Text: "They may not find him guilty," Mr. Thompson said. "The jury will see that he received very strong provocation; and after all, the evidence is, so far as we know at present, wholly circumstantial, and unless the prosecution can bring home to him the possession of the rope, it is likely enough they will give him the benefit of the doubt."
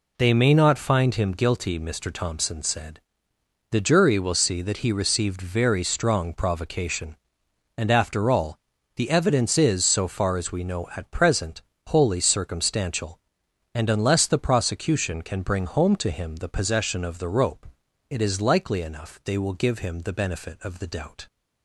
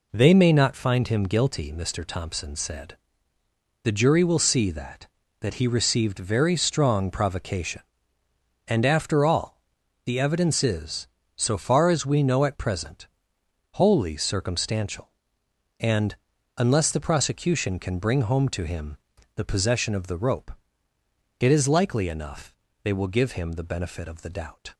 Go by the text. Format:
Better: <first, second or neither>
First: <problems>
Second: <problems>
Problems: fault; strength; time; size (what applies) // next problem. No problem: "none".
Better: first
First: none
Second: says "that" twice; at 5.3 s // pauses between "and" and "unless"; at 16.1 s; 0.42 s long // pauses between "him" and "the"; at 18.9 s; 0.38 s long // pauses between "enough" and "they"; slight; at 22.5 s; 0.30 s long